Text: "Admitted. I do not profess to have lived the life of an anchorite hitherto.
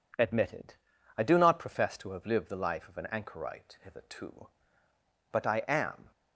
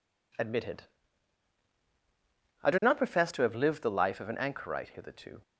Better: second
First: goes on to say "But I am"; noticeable; from 5.3 s on; 0.79 s long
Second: none

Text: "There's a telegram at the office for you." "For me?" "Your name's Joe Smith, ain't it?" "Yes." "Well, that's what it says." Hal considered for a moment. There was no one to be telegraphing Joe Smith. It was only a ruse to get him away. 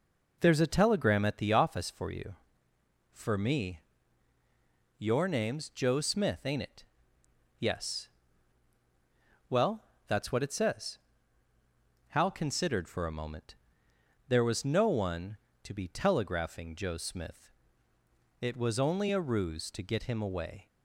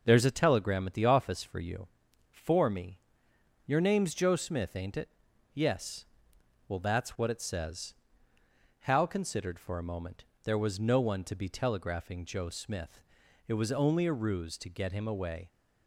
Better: neither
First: none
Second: none

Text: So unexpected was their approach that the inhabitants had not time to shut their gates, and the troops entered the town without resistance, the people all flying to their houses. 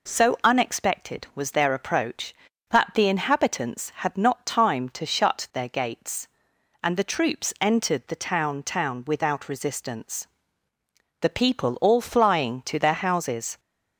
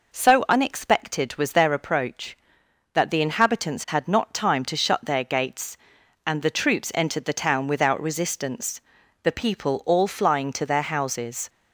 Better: second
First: says "town" twice; at 8.6 s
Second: none

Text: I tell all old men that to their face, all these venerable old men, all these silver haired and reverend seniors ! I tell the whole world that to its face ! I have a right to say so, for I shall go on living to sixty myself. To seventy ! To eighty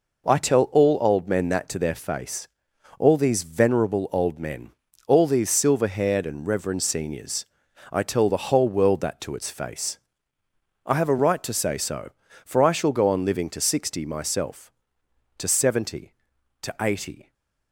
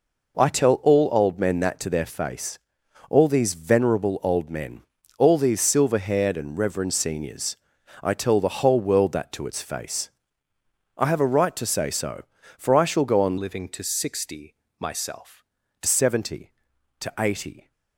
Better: first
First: none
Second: changes voice from "living" to "To"; from 13.3 to 15.8 s; 2.5 s long // pauses between "sixty" and "myself"; slight; at 14.5 s; 0.26 s long

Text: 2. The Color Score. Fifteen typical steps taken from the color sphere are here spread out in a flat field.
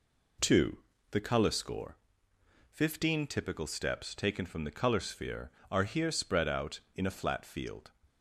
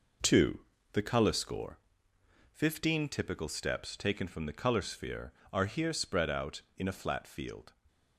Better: first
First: none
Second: gets quieter; throughout; 6.5 dB

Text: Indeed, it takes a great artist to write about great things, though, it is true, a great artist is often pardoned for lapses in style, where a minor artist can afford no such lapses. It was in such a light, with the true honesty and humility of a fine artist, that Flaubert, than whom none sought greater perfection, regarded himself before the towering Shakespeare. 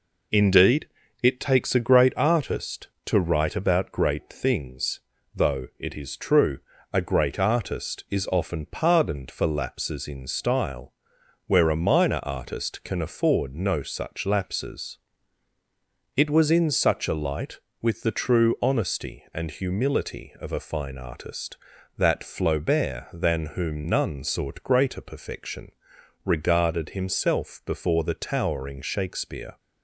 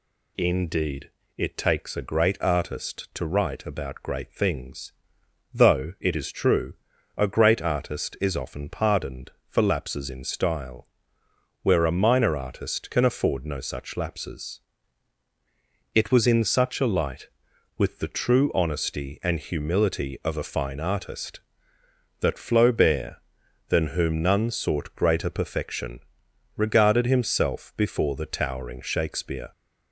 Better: neither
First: none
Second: none

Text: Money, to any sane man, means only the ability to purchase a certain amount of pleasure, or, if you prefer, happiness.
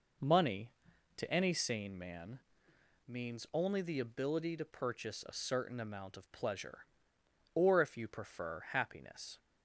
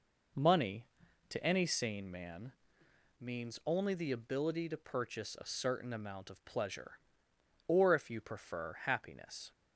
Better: neither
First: none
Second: none

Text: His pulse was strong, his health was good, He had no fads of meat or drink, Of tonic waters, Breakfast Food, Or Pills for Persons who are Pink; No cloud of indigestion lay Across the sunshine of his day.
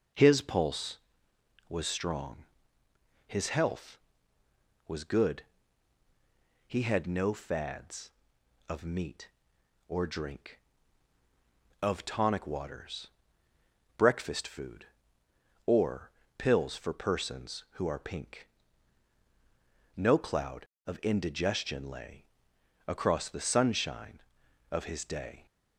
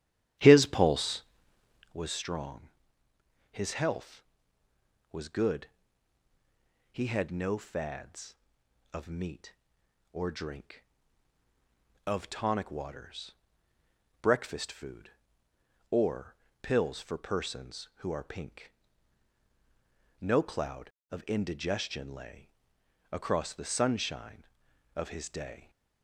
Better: first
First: pauses between "Or" and "Pills"; slight; at 16.1 s; 0.26 s long // pauses between "lay" and "Across"; noticeable; at 22.2 s; 0.62 s long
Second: starts louder than the rest; strong; until 2.0 s; 10.5 dB // pauses between "Or" and "Pills"; slight; at 16.3 s; 0.26 s long // pauses between "lay" and "Across"; noticeable; at 22.4 s; 0.62 s long

